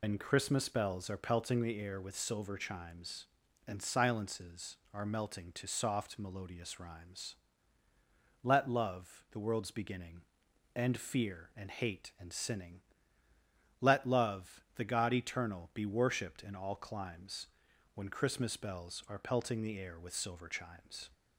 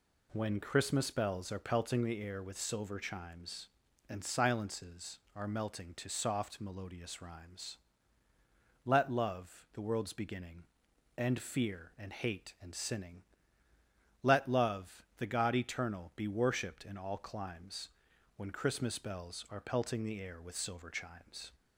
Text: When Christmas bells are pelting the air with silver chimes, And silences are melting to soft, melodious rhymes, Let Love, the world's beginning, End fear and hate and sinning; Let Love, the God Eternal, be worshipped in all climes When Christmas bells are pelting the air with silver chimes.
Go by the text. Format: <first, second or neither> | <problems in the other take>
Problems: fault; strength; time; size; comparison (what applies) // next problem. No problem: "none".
second | loses the start of "When"; at 0.0 s; 135 ms // pauses between "climes" and "When"; noticeable; at 17.4 s; 0.48 s long; noticeable in the second